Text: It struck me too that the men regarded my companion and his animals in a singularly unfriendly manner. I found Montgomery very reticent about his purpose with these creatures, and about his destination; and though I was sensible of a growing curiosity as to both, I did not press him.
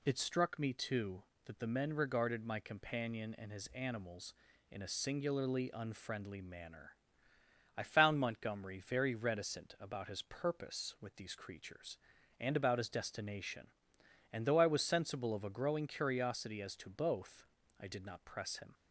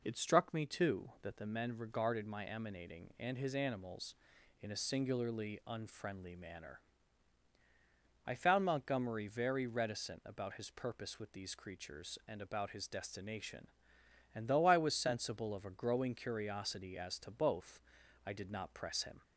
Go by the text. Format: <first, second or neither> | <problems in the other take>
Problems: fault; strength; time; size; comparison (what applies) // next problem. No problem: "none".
first | says "emanating" for "companion"; at 2.4 s